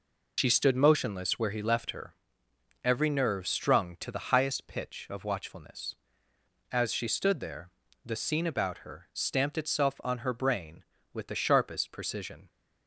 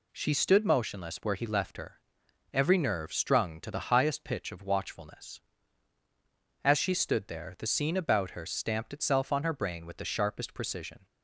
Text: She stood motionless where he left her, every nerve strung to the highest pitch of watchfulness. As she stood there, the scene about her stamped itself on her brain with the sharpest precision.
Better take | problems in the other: second | loses the start of "She"; at 0.3 s; 100 ms

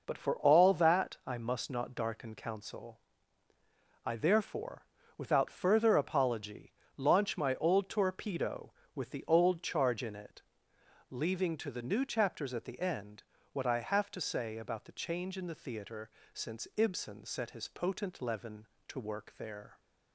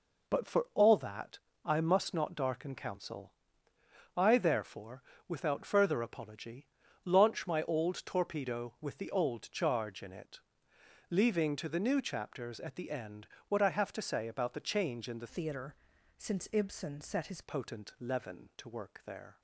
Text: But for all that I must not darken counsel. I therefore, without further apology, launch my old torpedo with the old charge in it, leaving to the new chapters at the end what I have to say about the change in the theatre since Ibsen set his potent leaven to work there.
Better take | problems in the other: first | pauses between "that" and "I"; slight; at 1.3 s; 0.26 s long // pauses between "end" and "what"; slight; at 13.2 s; 0.22 s long; slight in the first // changes voice from "theatre" to "his"; from 15.2 to 17.4 s; 2.2 s long // pauses between "theatre" and "since"; at 15.7 s; 0.44 s long; slight in the first

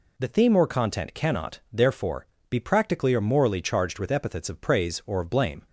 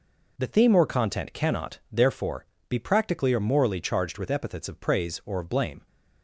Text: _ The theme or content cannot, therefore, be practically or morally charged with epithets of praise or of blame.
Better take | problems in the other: first | gets quieter; strong; throughout; 8.5 dB

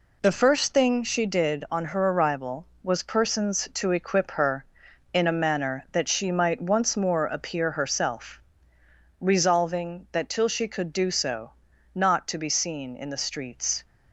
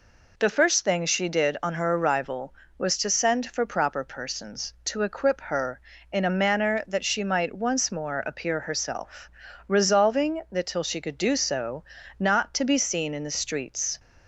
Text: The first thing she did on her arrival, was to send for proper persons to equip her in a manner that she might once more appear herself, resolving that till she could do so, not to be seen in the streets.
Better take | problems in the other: second | skips "to send for proper"; at 3.0 s

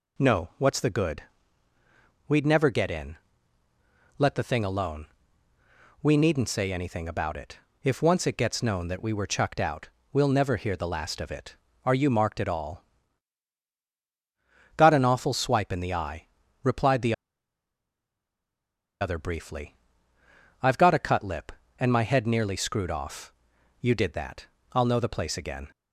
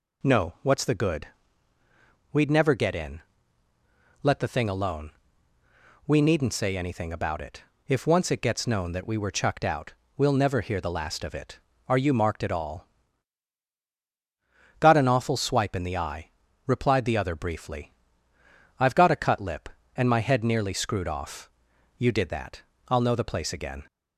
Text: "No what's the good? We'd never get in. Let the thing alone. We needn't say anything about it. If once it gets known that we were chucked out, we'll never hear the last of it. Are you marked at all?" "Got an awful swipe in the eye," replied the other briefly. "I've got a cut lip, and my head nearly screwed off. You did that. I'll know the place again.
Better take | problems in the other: second | pauses between "the" and "other"; strong; at 17.1 s; 1.8 s long

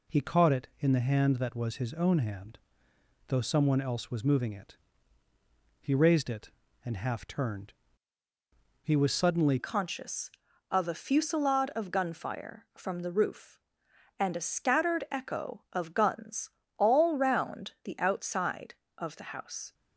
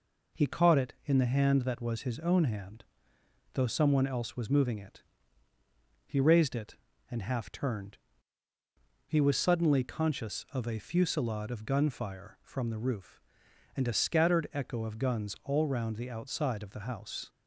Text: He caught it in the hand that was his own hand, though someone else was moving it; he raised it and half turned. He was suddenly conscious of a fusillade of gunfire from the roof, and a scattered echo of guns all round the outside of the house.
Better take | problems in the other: second | changes voice at "conscious"; from 9.5 s on; 10.2 s long // pauses between "guns" and "all"; slight; at 16.5 s; 0.26 s long

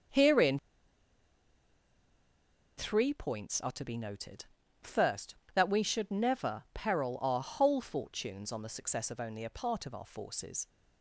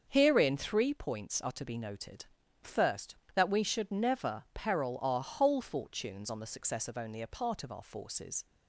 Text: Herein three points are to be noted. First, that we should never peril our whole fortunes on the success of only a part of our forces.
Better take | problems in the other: second | starts louder than the rest; until 3.3 s; 6.5 dB; also in the second // pauses between "Herein" and "three"; strong; at 0.5 s; 2.1 s long

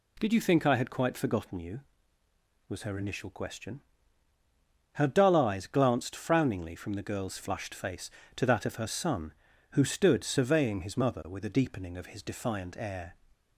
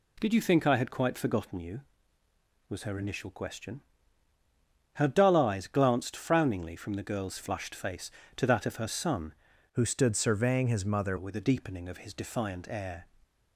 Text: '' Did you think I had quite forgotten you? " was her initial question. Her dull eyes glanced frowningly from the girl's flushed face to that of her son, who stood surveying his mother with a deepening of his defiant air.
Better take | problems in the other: first | changes voice from "who" to "mother"; from 9.7 to 11.1 s; 1.4 s long

